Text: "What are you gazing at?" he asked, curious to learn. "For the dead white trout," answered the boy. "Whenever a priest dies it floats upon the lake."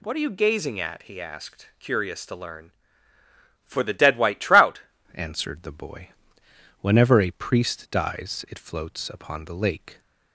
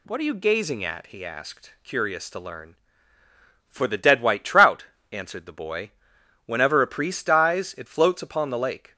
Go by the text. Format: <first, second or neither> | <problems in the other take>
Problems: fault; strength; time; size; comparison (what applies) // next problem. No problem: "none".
second | changes voice at "answered"; from 5.1 s on; 4.8 s long